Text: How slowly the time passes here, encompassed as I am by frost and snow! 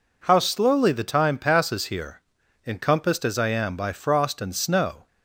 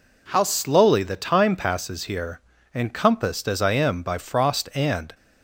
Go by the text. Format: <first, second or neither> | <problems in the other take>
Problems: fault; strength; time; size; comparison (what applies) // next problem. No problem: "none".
first | stops before "snow"; at 5.1 s